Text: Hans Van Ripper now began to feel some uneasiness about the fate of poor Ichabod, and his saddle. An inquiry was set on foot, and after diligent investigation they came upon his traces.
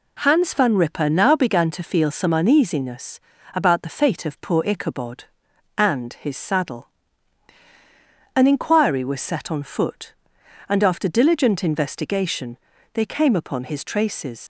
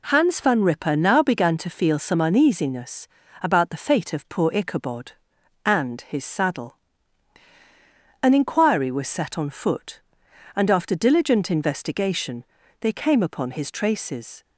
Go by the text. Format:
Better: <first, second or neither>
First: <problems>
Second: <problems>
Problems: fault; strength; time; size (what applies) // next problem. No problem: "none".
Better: second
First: pauses between "uneasiness" and "about"; slight; at 3.2 s; 0.34 s long // pauses between "investigation" and "they"; at 12.5 s; 0.38 s long // leaves "traces" unfinished; at 14.4 s; 95 ms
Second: pauses between "uneasiness" and "about"; slight; at 3.0 s; 0.34 s long // pauses between "investigation" and "they"; at 12.4 s; 0.38 s long